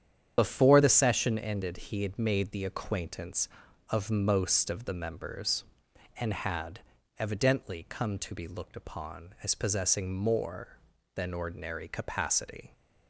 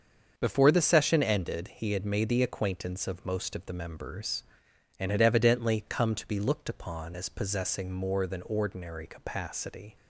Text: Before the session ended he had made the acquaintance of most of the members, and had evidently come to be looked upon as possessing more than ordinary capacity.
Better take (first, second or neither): second